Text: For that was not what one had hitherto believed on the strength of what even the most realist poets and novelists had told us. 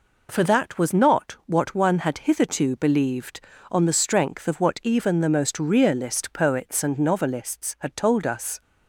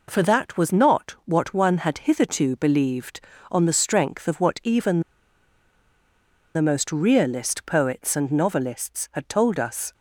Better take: first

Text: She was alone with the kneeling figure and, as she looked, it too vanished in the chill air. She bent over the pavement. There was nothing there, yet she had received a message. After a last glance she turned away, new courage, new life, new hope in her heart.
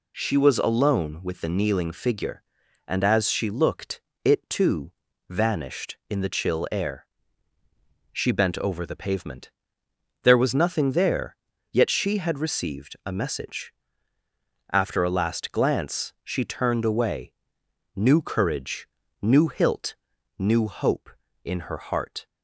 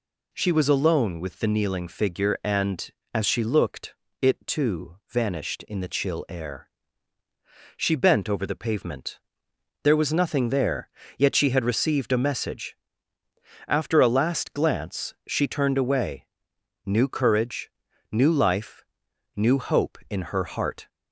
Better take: second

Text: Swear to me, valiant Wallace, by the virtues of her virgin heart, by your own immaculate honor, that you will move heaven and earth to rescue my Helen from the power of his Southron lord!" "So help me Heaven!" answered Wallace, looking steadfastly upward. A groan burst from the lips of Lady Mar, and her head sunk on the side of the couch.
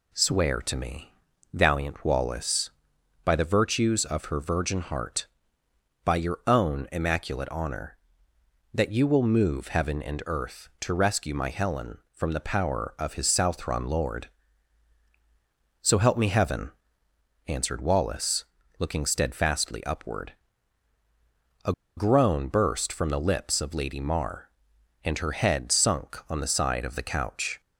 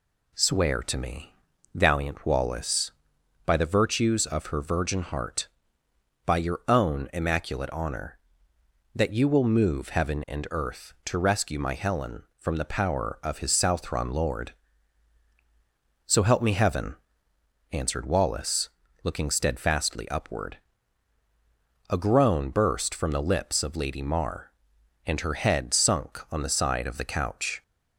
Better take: second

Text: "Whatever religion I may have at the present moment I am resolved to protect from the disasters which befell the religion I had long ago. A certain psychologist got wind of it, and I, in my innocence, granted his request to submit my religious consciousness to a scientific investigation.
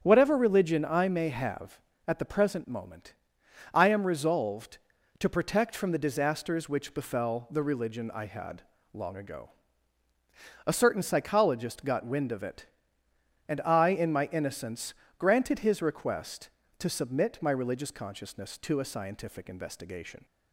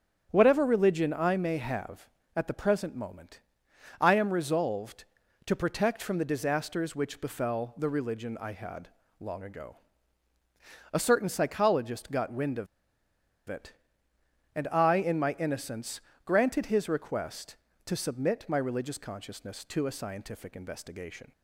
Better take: first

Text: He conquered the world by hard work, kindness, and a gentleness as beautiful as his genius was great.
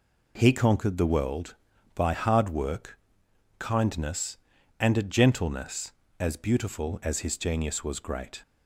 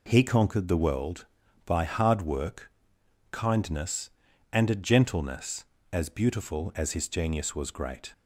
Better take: neither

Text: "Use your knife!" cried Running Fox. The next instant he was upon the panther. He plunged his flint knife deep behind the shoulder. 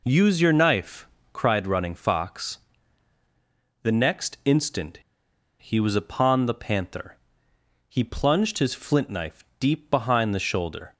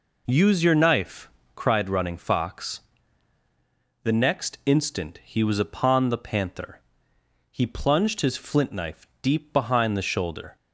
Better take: second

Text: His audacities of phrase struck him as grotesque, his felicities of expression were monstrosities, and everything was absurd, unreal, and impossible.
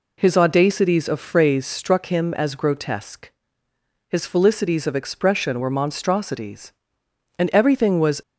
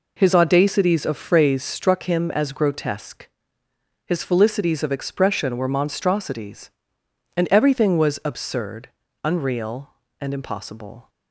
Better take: second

